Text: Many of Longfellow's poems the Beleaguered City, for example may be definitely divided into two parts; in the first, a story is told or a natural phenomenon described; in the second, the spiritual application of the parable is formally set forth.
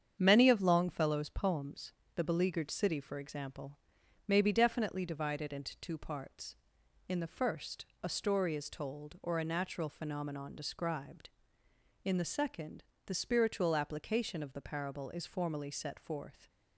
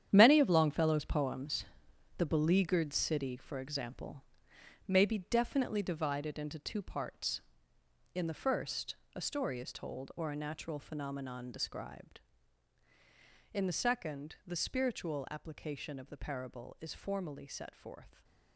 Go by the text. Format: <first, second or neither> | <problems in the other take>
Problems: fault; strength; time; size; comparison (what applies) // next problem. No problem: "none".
first | gets quieter; strong; throughout; 11 dB // starts louder than the rest; strong; until 1.1 s; 9.5 dB; strong in the first // pauses between "poems" and "the"; noticeable; at 1.6 s; 0.52 s long; slight in the first // pauses between "example" and "may"; noticeable; at 4.2 s; 0.64 s long; noticeable in the first